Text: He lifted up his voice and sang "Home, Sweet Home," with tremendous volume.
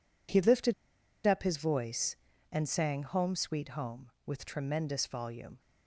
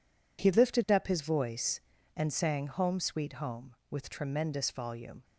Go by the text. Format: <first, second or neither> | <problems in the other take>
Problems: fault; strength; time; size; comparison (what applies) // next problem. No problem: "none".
second | pauses between "lifted" and "up"; noticeable; at 0.7 s; 0.54 s long